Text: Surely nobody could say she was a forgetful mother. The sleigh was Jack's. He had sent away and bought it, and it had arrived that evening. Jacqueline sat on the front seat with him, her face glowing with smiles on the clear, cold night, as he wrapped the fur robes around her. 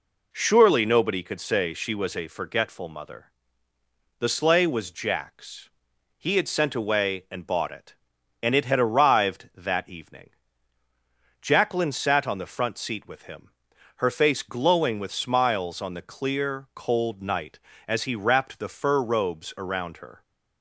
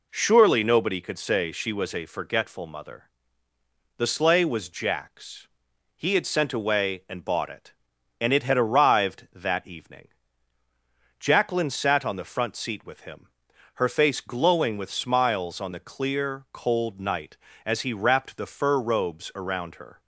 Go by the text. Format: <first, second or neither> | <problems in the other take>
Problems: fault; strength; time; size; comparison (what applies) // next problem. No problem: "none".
neither | none